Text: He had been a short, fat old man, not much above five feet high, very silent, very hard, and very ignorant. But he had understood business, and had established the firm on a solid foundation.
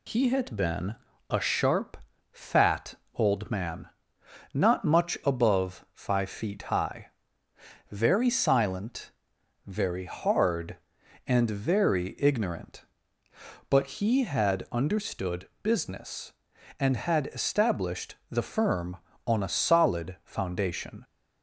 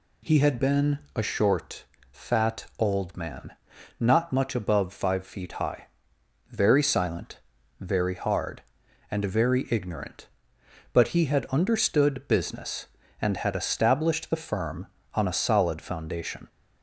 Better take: second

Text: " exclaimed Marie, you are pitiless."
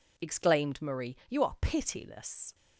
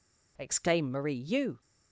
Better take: first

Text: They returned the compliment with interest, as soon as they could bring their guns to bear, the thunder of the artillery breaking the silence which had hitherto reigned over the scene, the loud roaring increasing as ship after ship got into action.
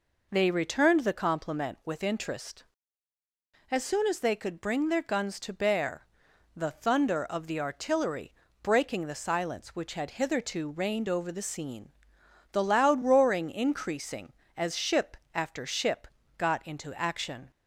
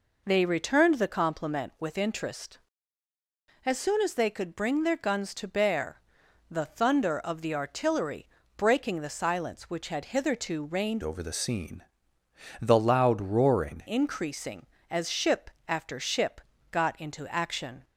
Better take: first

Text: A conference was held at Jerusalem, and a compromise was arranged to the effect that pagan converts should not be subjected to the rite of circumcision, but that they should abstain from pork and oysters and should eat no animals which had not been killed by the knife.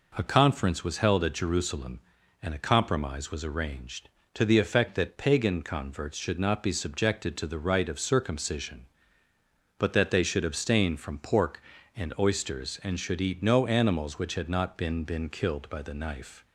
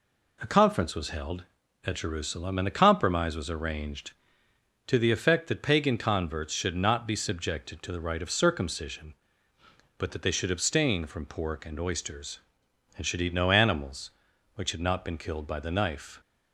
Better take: second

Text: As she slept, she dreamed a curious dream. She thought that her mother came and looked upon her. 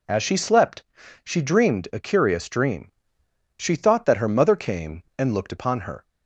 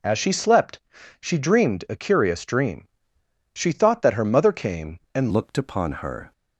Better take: first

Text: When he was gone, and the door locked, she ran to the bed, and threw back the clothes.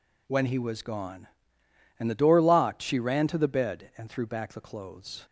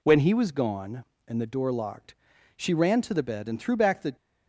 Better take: first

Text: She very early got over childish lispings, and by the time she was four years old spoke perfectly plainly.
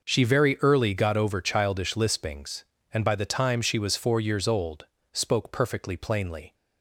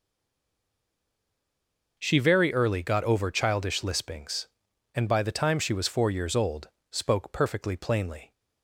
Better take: first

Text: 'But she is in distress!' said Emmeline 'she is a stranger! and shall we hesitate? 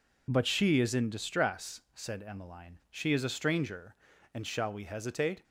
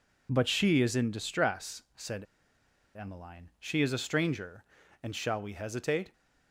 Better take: first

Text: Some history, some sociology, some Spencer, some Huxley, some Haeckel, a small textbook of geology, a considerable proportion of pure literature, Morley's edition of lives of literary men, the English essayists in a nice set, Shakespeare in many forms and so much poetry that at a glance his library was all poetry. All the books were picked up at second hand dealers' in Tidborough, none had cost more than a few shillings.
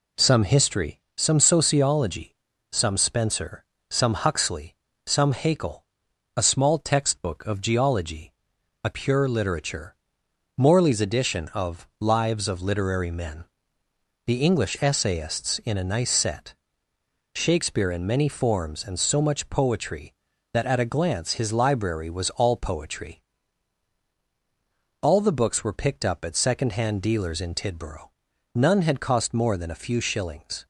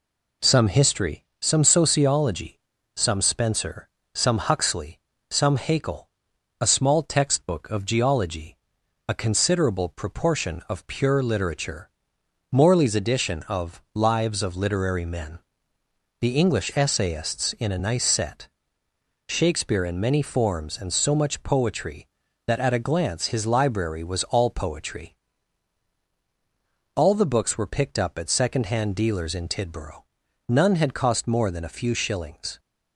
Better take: second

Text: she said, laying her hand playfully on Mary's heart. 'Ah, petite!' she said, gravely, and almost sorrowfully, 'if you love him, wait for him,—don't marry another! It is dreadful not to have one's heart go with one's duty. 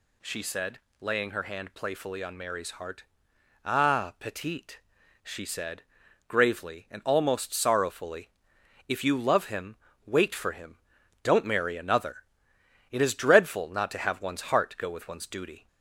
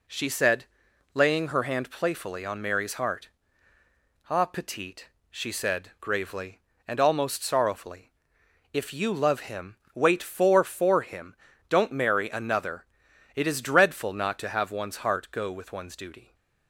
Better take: first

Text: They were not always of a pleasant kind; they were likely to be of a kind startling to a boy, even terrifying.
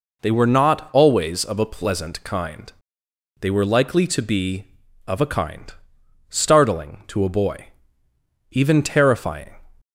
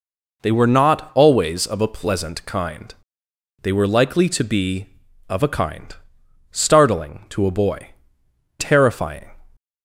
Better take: first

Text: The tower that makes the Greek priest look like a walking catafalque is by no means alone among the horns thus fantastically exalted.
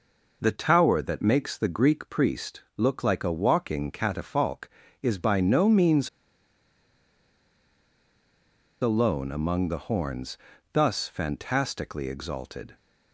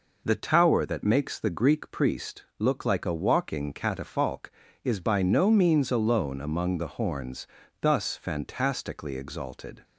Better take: second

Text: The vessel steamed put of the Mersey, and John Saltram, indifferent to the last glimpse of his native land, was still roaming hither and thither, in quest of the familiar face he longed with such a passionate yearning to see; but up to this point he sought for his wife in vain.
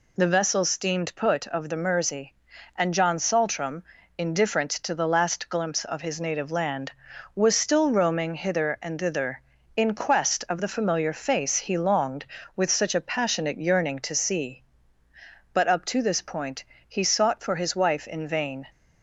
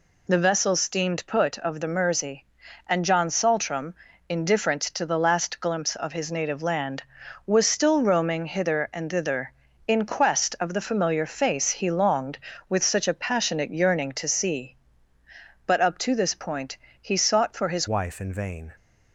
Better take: first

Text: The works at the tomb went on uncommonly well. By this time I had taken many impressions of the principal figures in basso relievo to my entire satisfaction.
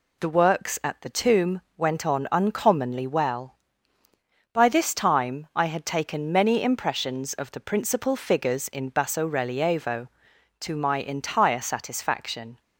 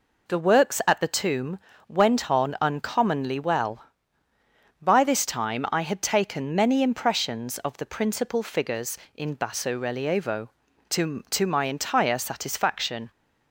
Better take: first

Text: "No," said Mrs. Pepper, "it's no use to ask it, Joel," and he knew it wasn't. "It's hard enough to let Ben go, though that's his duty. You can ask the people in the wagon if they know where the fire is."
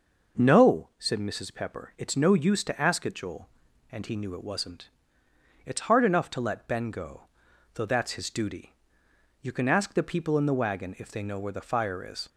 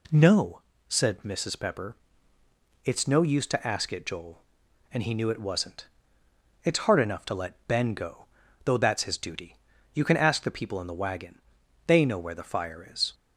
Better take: first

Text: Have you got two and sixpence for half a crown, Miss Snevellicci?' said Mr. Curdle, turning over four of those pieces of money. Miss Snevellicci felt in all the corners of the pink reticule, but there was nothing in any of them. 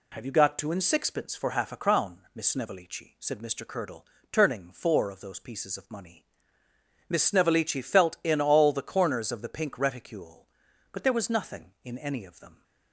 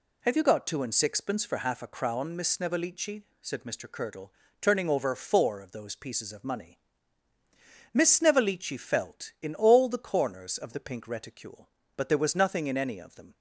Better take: second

